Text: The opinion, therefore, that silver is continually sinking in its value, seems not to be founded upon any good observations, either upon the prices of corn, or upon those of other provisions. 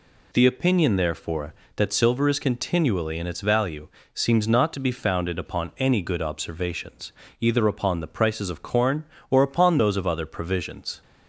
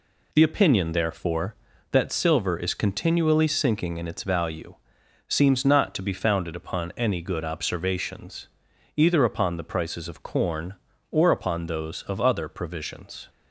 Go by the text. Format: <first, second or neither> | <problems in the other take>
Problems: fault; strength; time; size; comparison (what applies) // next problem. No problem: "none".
second | skips "sinking"; at 3.1 s